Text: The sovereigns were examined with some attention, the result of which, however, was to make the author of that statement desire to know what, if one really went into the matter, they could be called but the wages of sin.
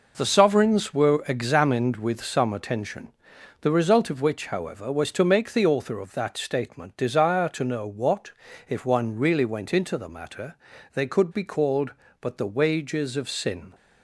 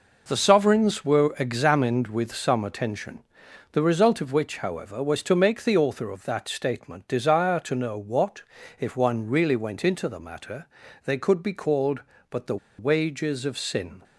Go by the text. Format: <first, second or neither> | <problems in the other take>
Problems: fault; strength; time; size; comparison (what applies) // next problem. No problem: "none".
first | pauses between "the" and "wages"; slight; at 12.5 s; 0.21 s long